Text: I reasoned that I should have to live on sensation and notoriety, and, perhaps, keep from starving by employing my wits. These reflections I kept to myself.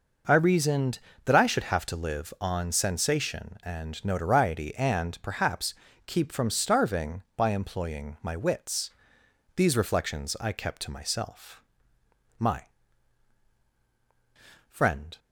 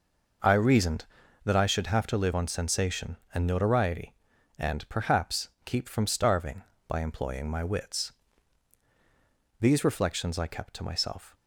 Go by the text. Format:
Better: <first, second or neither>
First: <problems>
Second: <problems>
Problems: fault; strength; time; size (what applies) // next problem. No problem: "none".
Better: second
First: goes on to say "My friend"; strong; from 12.3 s on; 2.8 s long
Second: none